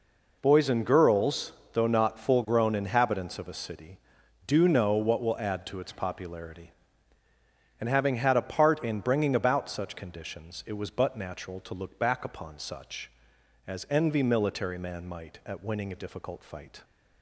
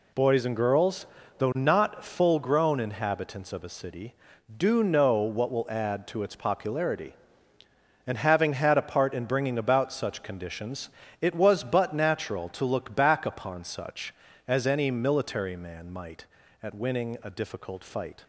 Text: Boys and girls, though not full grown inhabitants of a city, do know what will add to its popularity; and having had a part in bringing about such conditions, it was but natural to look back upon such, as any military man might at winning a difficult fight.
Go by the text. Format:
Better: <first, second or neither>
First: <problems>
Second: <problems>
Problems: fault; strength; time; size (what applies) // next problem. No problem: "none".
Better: second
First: says "envy" for "any"; at 13.8 s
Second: none